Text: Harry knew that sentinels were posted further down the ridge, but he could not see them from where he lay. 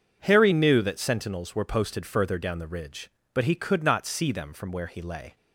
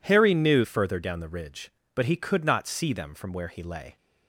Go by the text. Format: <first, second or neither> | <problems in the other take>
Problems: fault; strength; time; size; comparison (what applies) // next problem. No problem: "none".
first | skips "that sentinels were posted"; at 0.6 s